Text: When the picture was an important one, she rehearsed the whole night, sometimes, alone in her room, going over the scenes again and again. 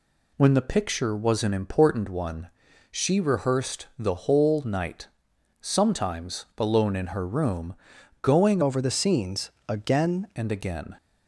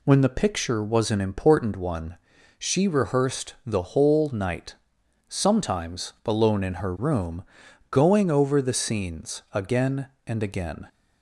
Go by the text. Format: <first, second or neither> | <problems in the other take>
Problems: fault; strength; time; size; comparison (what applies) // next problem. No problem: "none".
second | changes voice from "over" to "again"; from 8.6 to 10.2 s; 1.6 s long // pauses between "scenes" and "again"; slight; at 9.5 s; 0.16 s long